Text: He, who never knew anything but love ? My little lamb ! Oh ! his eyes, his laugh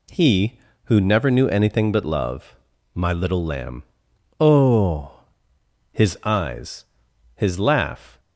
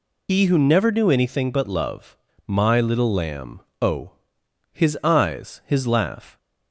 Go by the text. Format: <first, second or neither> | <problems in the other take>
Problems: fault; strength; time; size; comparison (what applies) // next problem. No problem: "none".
first | loses the start of "He"; at 0.2 s; 105 ms